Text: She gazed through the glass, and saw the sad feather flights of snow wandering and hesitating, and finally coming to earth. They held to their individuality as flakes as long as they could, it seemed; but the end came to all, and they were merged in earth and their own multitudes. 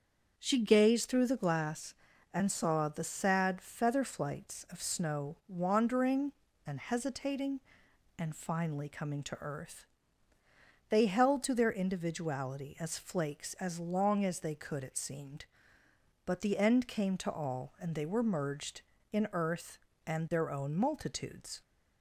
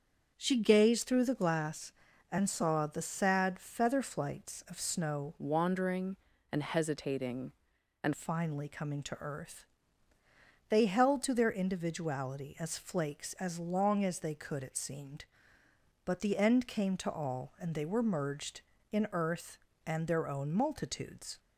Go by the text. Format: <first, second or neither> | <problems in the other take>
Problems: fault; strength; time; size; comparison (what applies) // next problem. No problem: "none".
first | starts louder than the rest; until 1.3 s; 7 dB; also in the first // changes voice from "wandering" to "and"; from 5.3 to 8.1 s; 2.8 s long